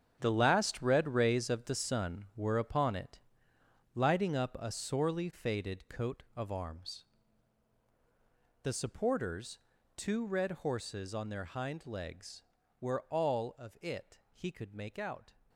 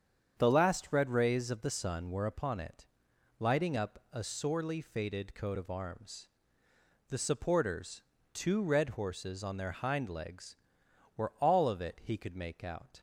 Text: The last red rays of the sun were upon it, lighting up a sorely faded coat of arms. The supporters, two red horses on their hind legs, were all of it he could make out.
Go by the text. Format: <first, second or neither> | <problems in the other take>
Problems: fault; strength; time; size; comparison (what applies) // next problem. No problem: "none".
second | gets quieter; strong; throughout; 12 dB // starts louder than the rest; strong; until 1.2 s; 8.5 dB; strong in the second